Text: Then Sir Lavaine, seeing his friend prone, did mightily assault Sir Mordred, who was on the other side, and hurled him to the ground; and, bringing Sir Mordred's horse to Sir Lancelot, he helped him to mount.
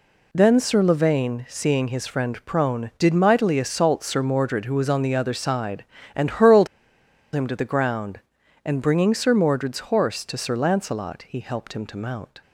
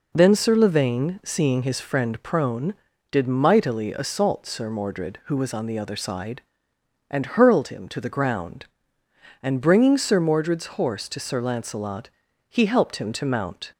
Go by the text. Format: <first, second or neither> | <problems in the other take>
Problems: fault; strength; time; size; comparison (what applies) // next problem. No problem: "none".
second | pauses between "hurled" and "him"; noticeable; at 6.6 s; 0.67 s long